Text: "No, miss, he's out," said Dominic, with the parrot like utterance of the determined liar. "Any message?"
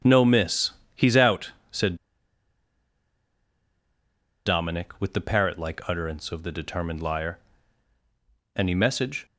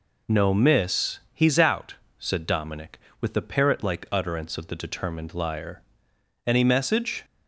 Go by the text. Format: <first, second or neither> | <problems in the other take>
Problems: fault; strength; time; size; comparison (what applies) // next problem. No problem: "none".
second | starts louder than the rest; strong; until 1.3 s; 9 dB // pauses between "said" and "Dominic"; strong; at 1.9 s; 2.5 s long